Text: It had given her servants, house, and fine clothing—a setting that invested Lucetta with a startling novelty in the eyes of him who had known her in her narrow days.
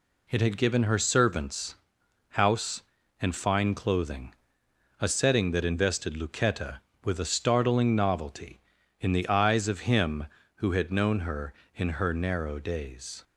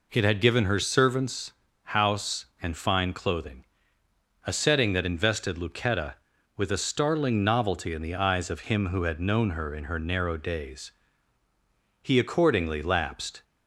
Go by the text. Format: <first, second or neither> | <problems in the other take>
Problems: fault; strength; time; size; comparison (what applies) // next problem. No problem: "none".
first | goes on to say "He accordingly lapsed"; from 12.0 s on; 1.4 s long